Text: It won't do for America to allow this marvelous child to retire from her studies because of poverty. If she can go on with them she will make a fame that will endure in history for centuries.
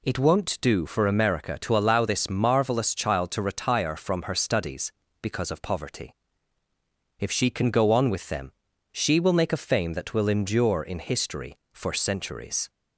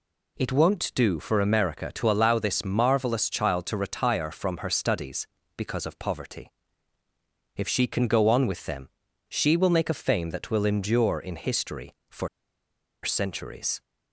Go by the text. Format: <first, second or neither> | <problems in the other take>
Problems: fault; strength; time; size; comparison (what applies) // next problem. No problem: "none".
first | pauses between "them" and "she"; at 8.8 s; 0.40 s long; also in the first // pauses between "for" and "centuries"; noticeable; at 12.2 s; 0.74 s long